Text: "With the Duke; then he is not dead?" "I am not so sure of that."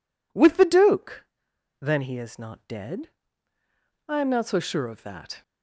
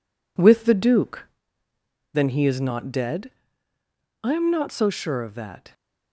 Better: first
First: none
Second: gets quieter; throughout; 6.5 dB

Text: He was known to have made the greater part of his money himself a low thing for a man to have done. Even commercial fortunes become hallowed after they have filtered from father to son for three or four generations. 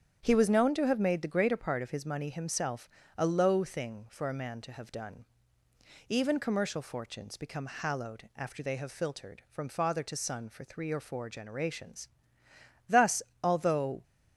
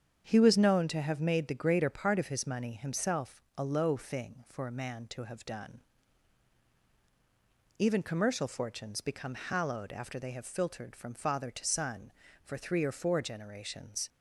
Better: second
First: starts louder than the rest; strong; until 1.2 s; 8.5 dB // pauses between "himself" and "a"; slight; at 2.8 s; 0.28 s long // goes on to say "Thus although"; noticeable; from 12.8 s on; 1.1 s long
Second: starts louder than the rest; strong; until 1.2 s; 8 dB // pauses between "himself" and "a"; slight; at 3.4 s; 0.16 s long

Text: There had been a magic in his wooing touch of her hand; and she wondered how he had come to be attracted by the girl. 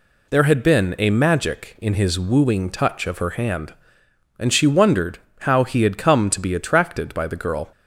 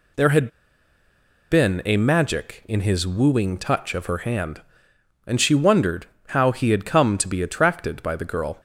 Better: first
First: pauses between "wondered" and "how"; slight; at 5.1 s; 0.22 s long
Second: pauses between "had" and "been"; at 0.4 s; 1.0 s long // pauses between "wondered" and "how"; slight; at 6.0 s; 0.22 s long

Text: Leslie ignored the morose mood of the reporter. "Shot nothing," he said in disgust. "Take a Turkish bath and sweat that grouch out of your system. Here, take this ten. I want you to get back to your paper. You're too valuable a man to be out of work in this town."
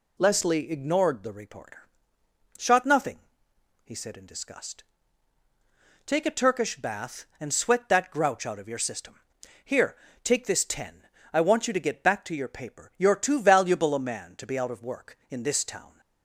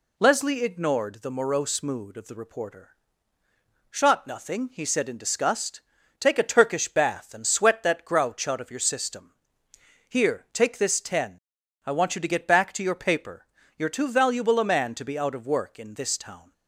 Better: second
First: skips "the morose mood of"; at 1.2 s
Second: none

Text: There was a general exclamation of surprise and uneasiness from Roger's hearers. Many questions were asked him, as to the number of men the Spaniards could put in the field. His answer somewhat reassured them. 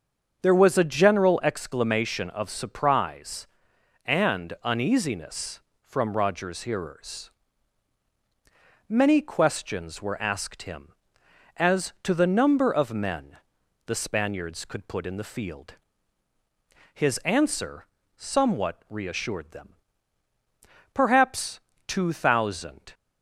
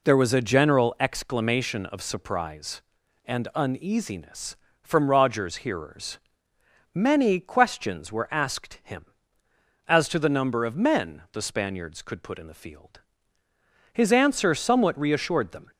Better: second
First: starts louder than the rest; until 1.4 s; 7 dB // pauses between "men" and "the"; noticeable; at 13.3 s; 0.50 s long // pauses between "answer" and "somewhat"; slight; at 17.8 s; 0.30 s long // goes on to say "Perhaps two thousand"; strong; from 20.9 s on; 2.0 s long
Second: none

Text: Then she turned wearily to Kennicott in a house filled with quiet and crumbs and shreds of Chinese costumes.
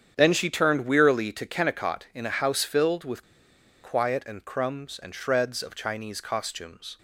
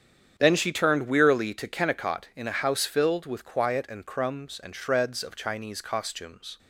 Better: second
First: starts louder than the rest; strong; until 1.1 s; 8.5 dB // pauses between "with" and "quiet"; noticeable; at 3.2 s; 0.60 s long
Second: starts louder than the rest; strong; until 1.4 s; 8.5 dB

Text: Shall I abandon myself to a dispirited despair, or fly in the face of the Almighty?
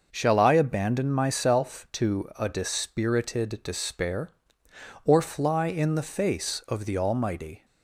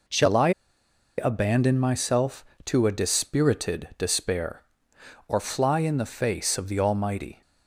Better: first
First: none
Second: pauses between "I" and "abandon"; noticeable; at 0.5 s; 0.67 s long

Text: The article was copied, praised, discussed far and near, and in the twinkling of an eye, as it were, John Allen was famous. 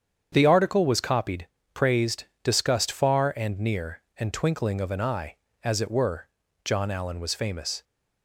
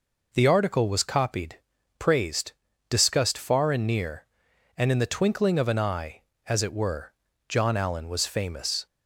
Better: second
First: starts louder than the rest; strong; until 1.3 s; 8 dB // skips "in the"; at 4.3 s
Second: none

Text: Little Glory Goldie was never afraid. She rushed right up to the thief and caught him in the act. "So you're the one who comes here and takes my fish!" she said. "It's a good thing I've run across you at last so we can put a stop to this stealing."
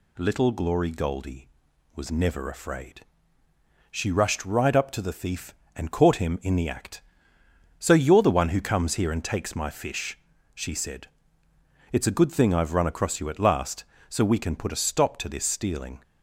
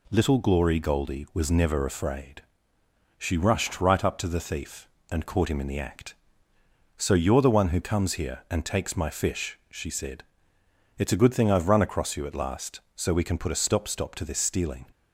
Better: first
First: none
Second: says "stop" twice; at 13.8 s

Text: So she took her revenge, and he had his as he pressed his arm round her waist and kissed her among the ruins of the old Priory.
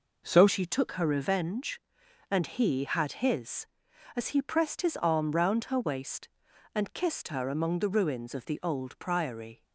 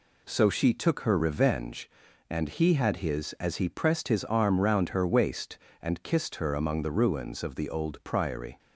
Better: second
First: changes voice at "she"; from 0.4 s on; 9.2 s long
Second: none

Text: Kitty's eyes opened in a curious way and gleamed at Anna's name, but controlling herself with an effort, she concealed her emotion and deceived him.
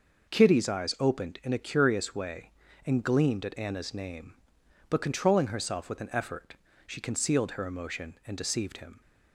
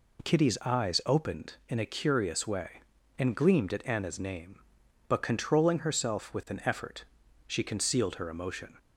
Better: first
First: none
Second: stops before "and deceived him"; at 8.7 s

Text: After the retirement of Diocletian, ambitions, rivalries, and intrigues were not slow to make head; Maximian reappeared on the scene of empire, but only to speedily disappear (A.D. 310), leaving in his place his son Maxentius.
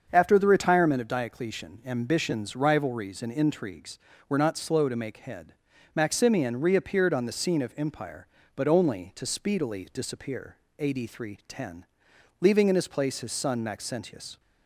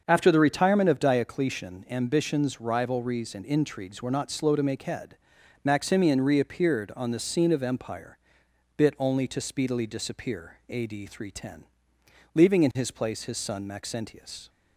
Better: first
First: starts louder than the rest; until 1.1 s; 7 dB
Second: starts louder than the rest; until 1.0 s; 6.5 dB // says "bit" for "but"; at 8.7 s

